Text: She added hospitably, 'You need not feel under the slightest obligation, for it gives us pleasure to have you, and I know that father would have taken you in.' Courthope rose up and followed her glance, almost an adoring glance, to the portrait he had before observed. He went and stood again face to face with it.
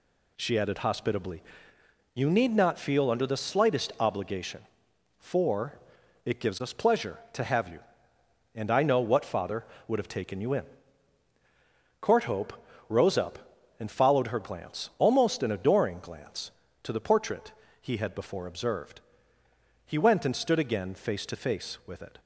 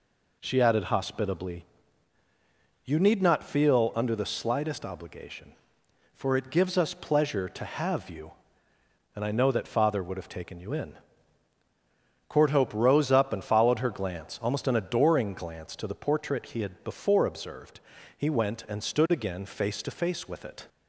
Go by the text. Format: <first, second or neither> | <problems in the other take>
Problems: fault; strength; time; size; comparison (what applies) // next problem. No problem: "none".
second | pauses between "for" and "it"; noticeable; at 5.7 s; 0.46 s long // says "what" for "that"; at 8.9 s // pauses between "Courthope" and "rose"; slight; at 12.5 s; 0.36 s long // pauses between "portrait" and "he"; slight; at 17.5 s; 0.30 s long